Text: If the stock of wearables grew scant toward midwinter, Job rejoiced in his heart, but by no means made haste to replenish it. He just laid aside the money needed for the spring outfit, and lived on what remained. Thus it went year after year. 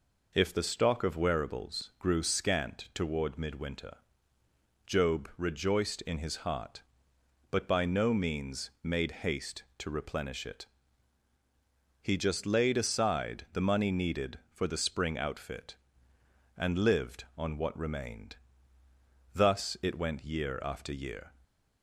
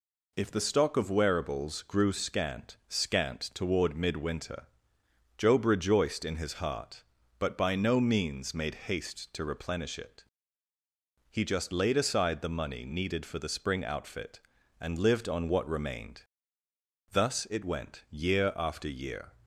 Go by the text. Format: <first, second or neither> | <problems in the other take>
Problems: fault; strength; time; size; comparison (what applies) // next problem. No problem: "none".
first | says "scant" twice; at 2.8 s